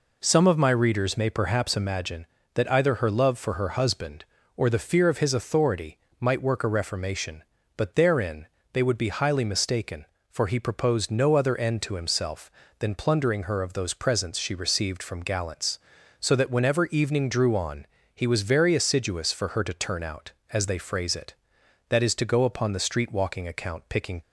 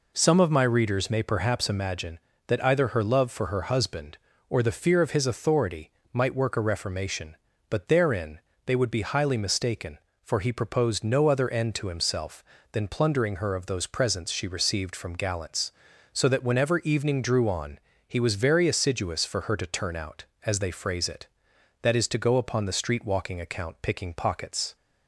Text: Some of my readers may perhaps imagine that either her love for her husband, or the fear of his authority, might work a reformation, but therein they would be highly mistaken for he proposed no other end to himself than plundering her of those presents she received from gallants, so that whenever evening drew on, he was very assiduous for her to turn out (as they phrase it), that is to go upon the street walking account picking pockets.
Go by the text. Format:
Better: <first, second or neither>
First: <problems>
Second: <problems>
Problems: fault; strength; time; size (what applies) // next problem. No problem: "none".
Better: second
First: pauses between "therein" and "they"; slight; at 8.4 s; 0.28 s long // stops before "pockets"; at 24.2 s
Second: pauses between "therein" and "they"; slight; at 8.3 s; 0.28 s long